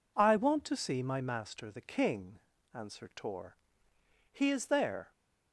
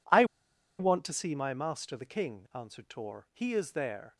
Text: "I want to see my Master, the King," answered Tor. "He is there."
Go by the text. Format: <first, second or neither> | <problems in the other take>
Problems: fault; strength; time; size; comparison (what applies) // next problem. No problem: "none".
first | pauses between "I" and "want"; noticeable; at 0.2 s; 0.55 s long